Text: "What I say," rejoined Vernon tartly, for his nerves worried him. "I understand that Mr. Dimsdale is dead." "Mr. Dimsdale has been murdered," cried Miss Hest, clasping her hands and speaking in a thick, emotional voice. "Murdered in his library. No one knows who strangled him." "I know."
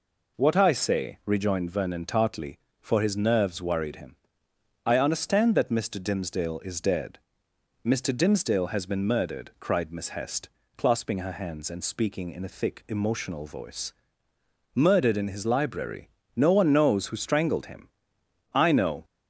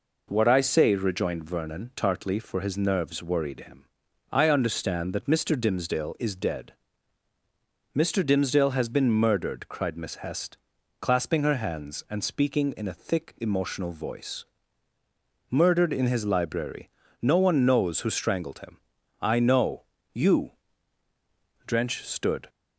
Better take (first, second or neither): first